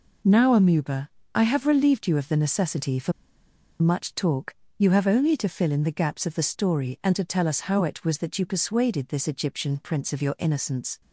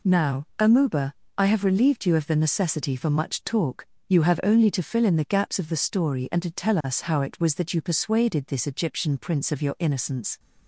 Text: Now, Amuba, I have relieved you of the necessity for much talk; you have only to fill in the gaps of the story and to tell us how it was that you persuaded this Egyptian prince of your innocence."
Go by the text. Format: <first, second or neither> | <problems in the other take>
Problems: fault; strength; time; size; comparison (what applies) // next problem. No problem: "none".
second | pauses between "for" and "much"; noticeable; at 3.1 s; 0.68 s long